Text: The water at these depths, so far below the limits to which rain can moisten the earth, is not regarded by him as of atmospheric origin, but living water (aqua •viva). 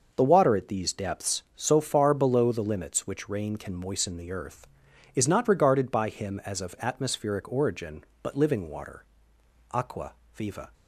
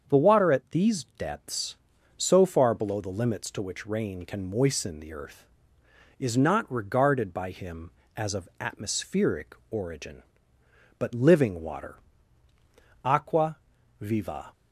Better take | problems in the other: second | starts louder than the rest; noticeable; until 1.1 s; 6 dB; strong in the second // skips "to"; at 3.0 s

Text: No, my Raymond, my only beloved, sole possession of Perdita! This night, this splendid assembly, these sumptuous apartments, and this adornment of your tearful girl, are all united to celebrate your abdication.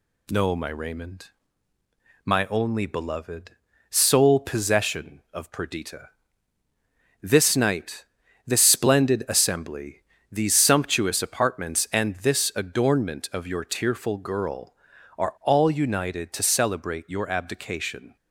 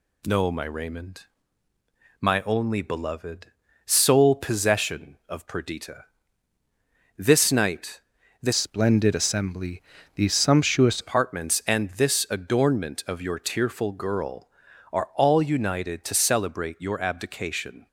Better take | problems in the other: first | changes voice from "splendid" to "sumptuous"; from 8.5 to 11.0 s; 2.5 s long

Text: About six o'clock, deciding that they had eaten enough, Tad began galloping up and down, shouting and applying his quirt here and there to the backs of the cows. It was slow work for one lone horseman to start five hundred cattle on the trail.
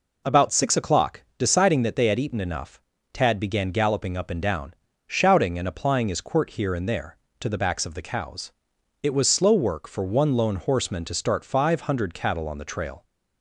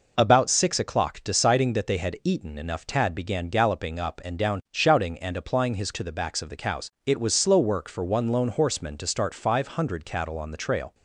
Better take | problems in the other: first | skips "quirt here and there"; at 5.9 s

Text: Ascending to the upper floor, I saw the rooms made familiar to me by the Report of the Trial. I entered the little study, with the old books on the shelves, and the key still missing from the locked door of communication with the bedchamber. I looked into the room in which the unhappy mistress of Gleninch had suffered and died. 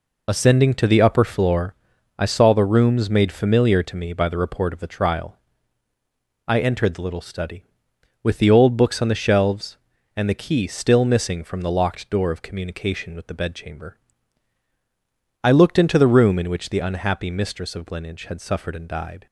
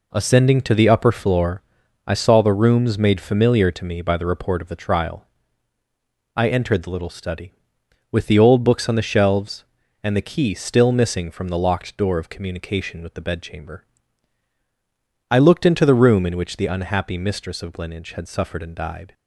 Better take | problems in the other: second | loses the start of "Ascending"; at 0.2 s; 30 ms

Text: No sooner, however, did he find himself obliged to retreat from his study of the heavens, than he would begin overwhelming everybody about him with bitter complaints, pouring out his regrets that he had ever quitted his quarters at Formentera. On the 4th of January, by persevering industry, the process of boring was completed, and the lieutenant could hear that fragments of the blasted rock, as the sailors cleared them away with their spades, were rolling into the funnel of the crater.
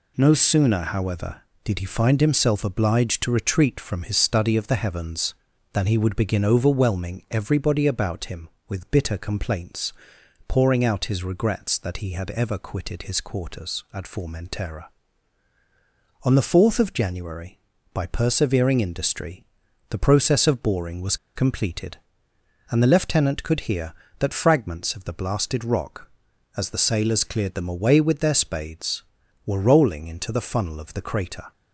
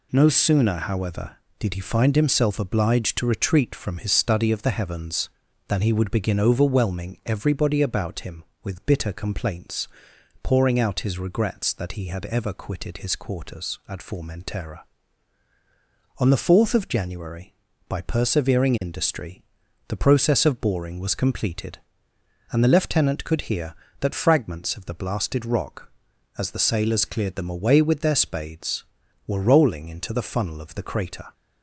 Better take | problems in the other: second | pauses between "was" and "completed"; slight; at 21.1 s; 0.19 s long

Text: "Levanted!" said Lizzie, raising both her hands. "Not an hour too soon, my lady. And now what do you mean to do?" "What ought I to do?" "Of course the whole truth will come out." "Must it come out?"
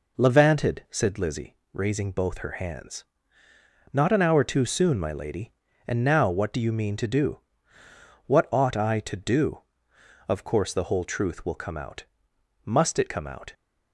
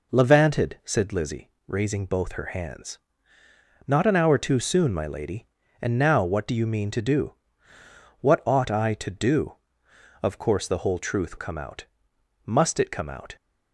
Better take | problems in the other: first | skips "will"; at 11.3 s

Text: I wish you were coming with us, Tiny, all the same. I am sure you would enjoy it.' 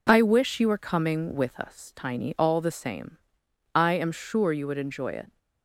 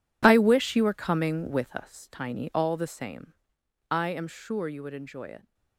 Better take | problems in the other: first | gets quieter; strong; throughout; 16.5 dB

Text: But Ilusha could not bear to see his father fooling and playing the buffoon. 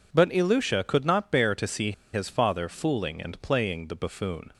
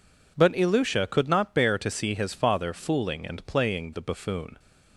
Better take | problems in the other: second | pauses between "see" and "his"; slight; at 1.9 s; 0.20 s long

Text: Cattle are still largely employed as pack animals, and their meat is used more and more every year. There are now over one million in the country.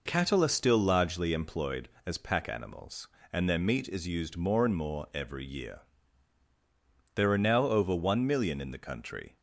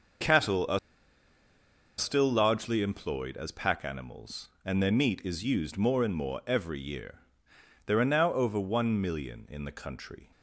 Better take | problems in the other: first | starts louder than the rest; until 2.4 s; 6.5 dB // pauses between "are" and "still"; at 0.7 s; 1.2 s long

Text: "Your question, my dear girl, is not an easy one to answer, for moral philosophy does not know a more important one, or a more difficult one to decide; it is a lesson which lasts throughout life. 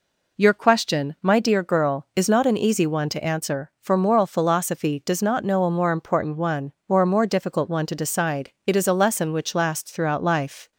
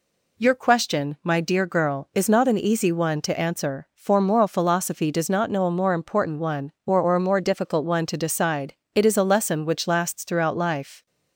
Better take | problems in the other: first | says "or" twice; at 6.9 s

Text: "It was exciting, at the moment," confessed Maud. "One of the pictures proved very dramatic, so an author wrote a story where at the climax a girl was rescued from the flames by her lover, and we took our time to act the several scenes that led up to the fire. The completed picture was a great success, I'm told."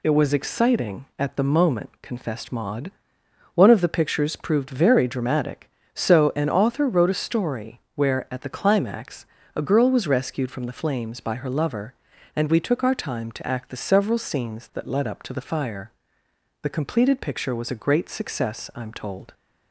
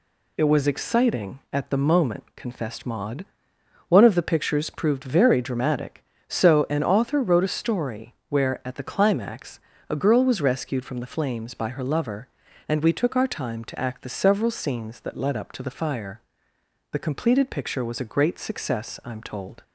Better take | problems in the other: neither | pauses between "story" and "where"; slight; the same in both // pauses between "climax" and "a"; slight; the same in both

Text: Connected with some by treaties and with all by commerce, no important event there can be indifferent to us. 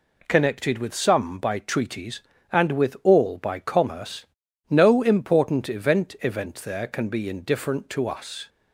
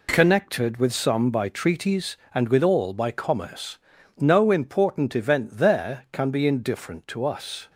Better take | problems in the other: second | says "event" twice; at 6.2 s

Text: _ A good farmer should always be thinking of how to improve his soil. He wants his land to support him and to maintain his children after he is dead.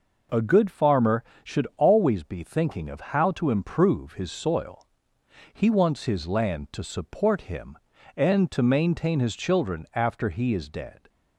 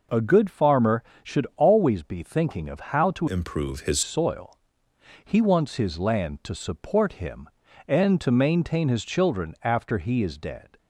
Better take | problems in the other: first | changes voice from "improve" to "his"; from 3.2 to 4.0 s; 0.8 s long

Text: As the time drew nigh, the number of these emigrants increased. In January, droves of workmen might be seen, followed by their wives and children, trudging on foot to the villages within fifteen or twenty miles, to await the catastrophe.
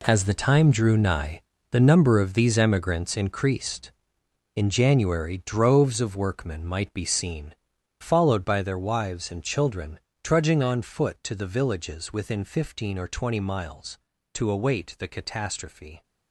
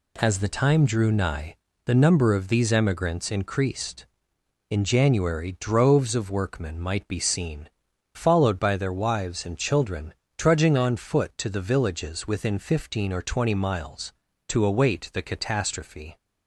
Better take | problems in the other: second | gets quieter; strong; throughout; 11.5 dB

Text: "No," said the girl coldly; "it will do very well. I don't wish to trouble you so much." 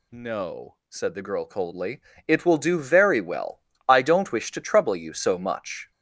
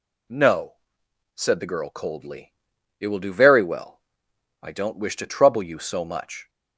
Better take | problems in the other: second | gets louder; noticeable; throughout; 6 dB

